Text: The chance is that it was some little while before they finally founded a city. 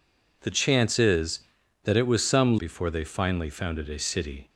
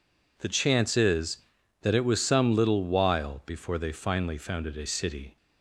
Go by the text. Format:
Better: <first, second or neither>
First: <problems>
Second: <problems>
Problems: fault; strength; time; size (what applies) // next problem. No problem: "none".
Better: second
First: skips "little while"; at 2.5 s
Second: none